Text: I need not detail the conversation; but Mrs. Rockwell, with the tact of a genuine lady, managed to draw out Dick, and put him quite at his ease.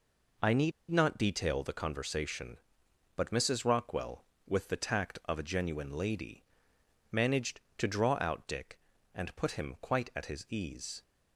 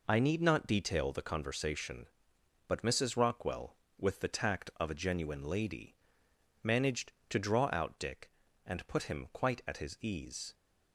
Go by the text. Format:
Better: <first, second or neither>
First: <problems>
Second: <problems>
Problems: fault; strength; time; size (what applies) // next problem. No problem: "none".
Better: second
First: pauses between "need" and "not"; slight; at 0.7 s; 0.18 s long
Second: none